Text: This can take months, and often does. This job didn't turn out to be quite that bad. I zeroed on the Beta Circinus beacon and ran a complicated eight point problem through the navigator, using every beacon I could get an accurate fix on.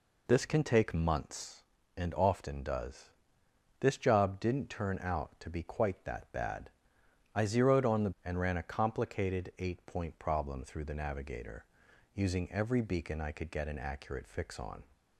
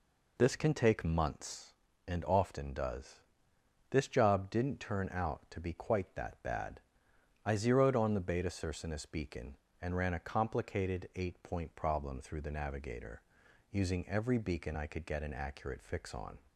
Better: second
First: skips "Beta Circinus beacon"; at 8.1 s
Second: none

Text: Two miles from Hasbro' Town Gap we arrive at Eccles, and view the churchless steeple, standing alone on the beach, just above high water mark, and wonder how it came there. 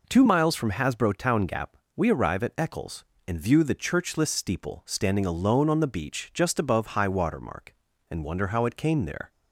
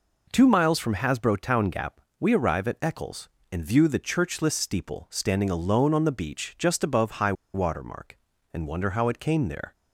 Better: first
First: pauses between "Gap" and "we"; slight; at 1.7 s; 0.20 s long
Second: pauses between "Gap" and "we"; slight; at 2.0 s; 0.20 s long // pauses between "high" and "water"; slight; at 7.3 s; 0.21 s long

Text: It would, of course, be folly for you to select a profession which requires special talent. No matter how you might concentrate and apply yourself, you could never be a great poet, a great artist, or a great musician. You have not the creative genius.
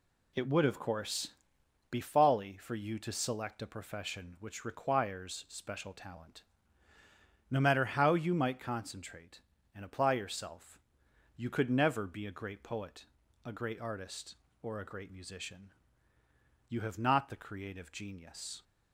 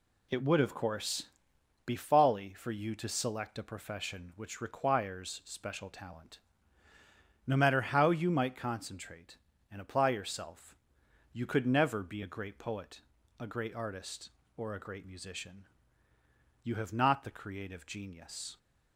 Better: neither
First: none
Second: none

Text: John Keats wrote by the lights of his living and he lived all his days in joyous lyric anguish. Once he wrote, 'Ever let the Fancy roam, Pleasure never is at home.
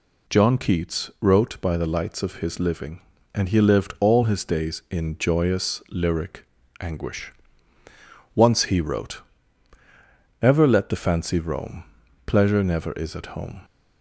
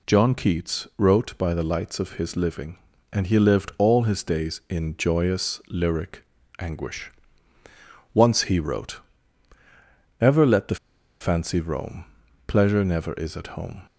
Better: first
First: pauses between "lyric" and "anguish"; slight; at 6.4 s; 0.36 s long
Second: pauses between "lyric" and "anguish"; slight; at 6.2 s; 0.36 s long // pauses between "the" and "Fancy"; at 10.7 s; 0.45 s long

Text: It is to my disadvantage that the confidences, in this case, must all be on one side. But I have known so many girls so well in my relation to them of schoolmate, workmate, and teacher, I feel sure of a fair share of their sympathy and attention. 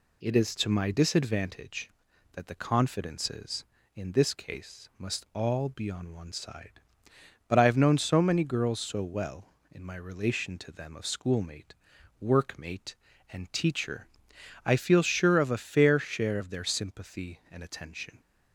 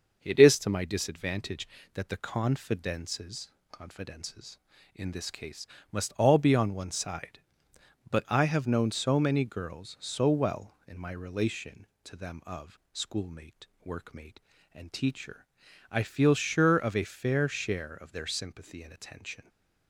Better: first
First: none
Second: starts louder than the rest; noticeable; until 1.2 s; 6 dB // says "confidences" twice; at 3.7 s

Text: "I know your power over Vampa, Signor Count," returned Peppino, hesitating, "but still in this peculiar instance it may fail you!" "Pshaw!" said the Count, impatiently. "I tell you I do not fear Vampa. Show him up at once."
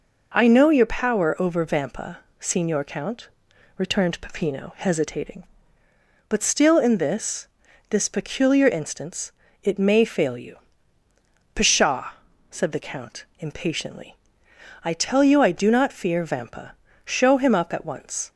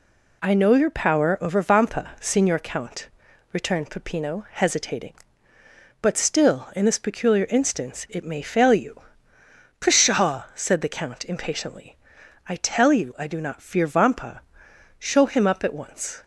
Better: second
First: says "this" twice; at 7.8 s // pauses between "instance" and "it"; slight; at 9.3 s; 0.28 s long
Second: none

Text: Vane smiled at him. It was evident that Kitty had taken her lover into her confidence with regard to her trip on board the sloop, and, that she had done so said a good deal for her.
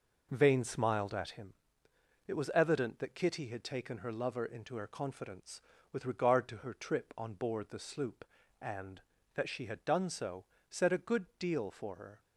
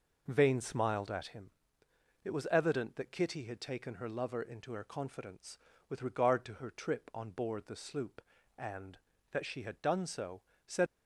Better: first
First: pauses between "so" and "said"; slight; at 10.4 s; 0.26 s long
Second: pauses between "so" and "said"; slight; at 10.4 s; 0.26 s long // stops before "a good deal for her"; at 10.8 s

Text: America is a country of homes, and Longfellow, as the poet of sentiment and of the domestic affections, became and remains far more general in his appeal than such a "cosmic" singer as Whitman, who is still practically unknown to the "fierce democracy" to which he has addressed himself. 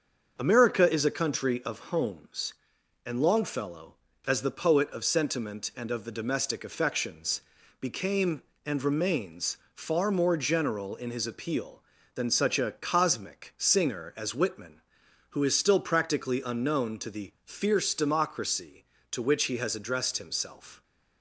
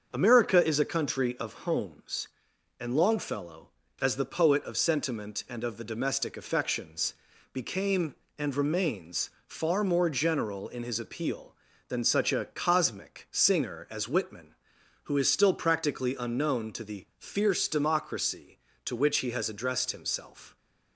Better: neither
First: starts louder than the rest; until 1.4 s; 6.5 dB // pauses between "remains" and "far"; slight; at 9.5 s; 0.16 s long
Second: starts louder than the rest; until 1.1 s; 6.5 dB // pauses between "remains" and "far"; slight; at 9.3 s; 0.16 s long

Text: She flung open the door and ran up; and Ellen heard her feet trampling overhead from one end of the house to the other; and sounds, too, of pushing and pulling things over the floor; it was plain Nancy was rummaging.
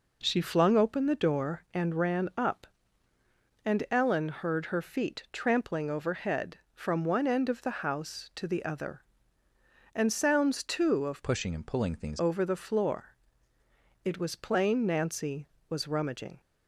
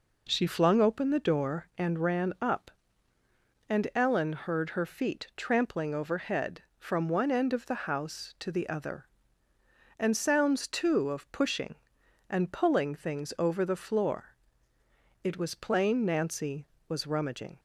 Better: second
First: changes voice from "pushing" to "things"; from 11.2 to 12.2 s; 1.0 s long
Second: none

